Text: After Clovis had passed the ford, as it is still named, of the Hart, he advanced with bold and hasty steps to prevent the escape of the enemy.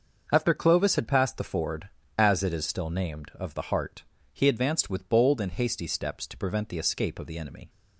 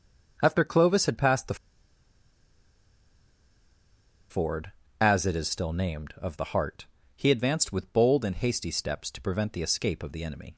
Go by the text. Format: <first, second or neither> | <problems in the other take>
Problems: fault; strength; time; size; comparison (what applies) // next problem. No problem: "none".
first | starts louder than the rest; until 1.4 s; 6 dB; also in the first // pauses between "the" and "ford"; strong; at 1.5 s; 2.7 s long